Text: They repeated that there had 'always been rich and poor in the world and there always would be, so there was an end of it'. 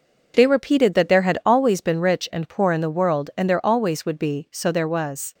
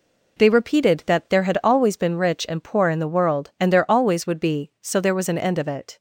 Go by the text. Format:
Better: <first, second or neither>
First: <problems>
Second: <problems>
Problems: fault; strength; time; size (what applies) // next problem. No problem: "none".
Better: second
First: stops before "an end of it"; at 5.3 s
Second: none